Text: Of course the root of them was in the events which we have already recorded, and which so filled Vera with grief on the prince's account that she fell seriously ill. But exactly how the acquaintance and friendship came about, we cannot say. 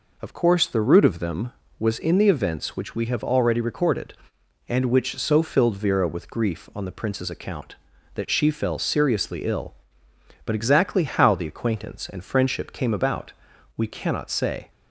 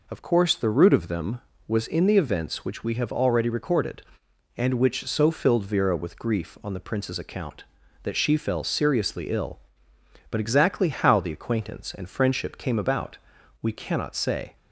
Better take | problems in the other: neither | none

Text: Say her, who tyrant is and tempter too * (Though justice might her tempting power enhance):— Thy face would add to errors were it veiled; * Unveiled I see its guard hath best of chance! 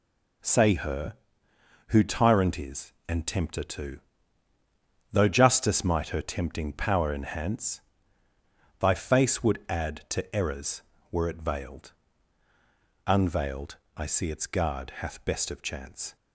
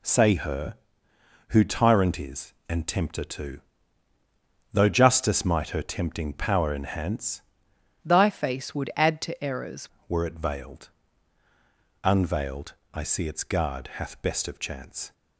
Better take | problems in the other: first | changes voice from "Thy" to "errors"; from 8.0 to 9.8 s; 1.8 s long // pauses between "Unveiled" and "I"; slight; at 12.7 s; 0.20 s long; slight in the first

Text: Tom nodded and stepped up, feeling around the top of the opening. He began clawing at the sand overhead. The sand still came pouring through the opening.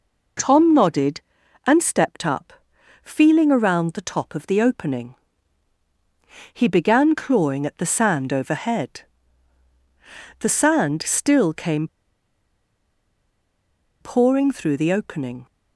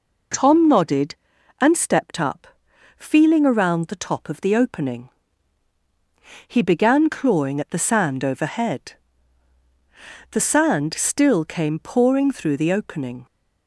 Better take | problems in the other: second | pauses between "came" and "pouring"; strong; at 11.8 s; 2.1 s long

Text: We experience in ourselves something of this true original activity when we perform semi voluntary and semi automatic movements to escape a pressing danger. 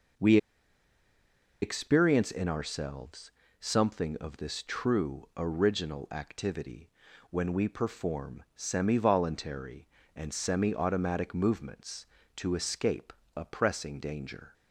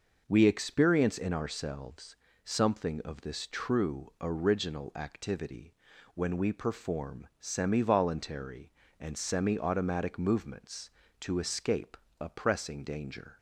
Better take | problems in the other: second | pauses between "We" and "experience"; strong; at 0.3 s; 1.2 s long // pauses between "ourselves" and "something"; slight; at 3.2 s; 0.30 s long; slight in the second // pauses between "activity" and "when"; at 6.8 s; 0.40 s long; also in the second // pauses between "escape" and "a"; slight; at 13.1 s; 0.22 s long; slight in the second

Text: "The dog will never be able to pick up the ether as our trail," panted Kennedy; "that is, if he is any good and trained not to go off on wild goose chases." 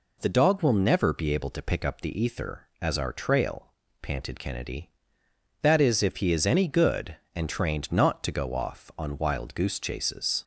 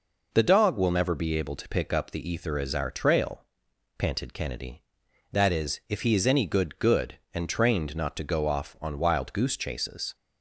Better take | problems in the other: first | says "good" twice; at 6.7 s

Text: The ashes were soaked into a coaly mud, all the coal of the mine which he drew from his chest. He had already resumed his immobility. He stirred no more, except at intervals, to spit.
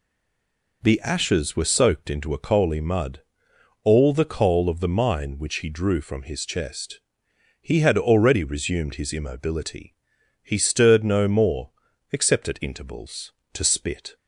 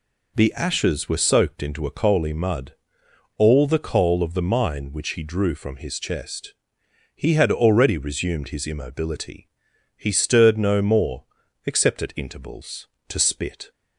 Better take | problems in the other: second | stays silent before the first word; slight; until 0.8 s; 0.8 s long

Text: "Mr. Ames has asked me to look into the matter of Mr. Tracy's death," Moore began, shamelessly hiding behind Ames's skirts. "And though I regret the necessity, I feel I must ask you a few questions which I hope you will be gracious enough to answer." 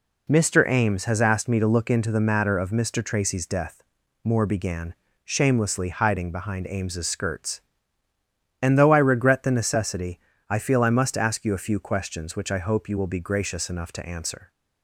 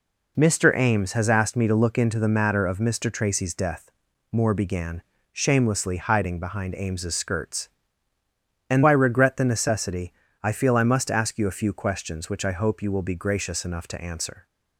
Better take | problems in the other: first | skips "though"; at 8.8 s

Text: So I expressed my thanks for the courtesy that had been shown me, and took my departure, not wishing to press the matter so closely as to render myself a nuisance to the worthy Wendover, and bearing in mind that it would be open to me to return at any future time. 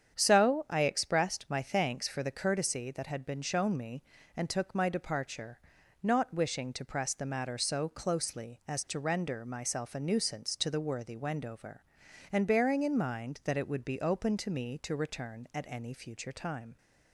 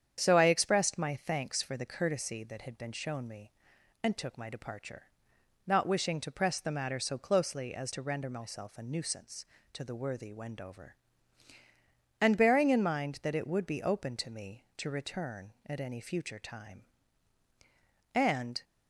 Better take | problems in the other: first | starts louder than the rest; strong; until 1.1 s; 8.5 dB; strong in the first // goes on to say "And"; slight; from 18.1 s on; 0.48 s long

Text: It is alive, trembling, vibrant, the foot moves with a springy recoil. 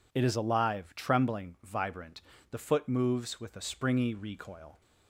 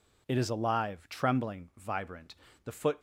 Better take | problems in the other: first | stops before "moves with a springy recoil"; at 2.9 s

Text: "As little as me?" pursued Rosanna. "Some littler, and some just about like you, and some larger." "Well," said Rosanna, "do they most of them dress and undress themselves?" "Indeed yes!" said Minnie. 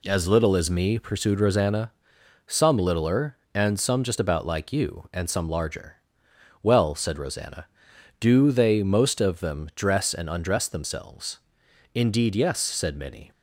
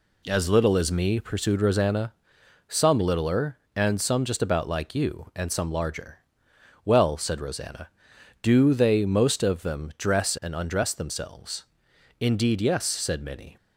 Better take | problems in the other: neither | none

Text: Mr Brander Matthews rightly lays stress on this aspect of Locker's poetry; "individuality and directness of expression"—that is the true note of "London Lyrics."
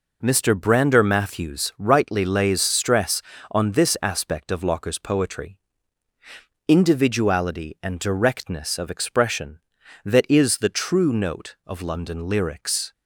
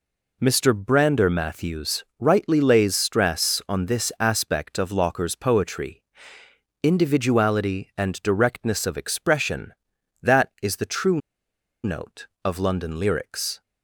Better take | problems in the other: first | pauses between "Matthews" and "rightly"; slight; at 2.0 s; 0.16 s long // pauses between "true" and "note"; noticeable; at 11.1 s; 0.65 s long

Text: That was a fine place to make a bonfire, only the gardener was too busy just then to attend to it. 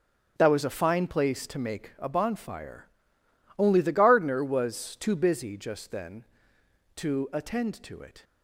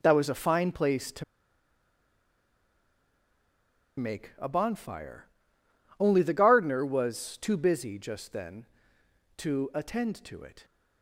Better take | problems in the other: first | starts louder than the rest; until 1.0 s; 6.5 dB; also in the first // pauses between "to" and "make"; strong; at 1.2 s; 2.7 s long

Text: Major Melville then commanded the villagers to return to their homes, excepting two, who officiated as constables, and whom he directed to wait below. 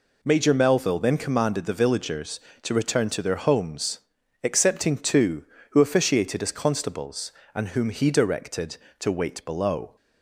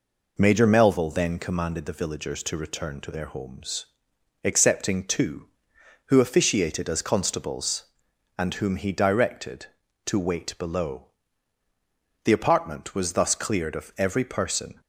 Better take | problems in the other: first | goes on to say "The apartment was thus cleared of every person"; strong; from 12.2 s on; 2.5 s long

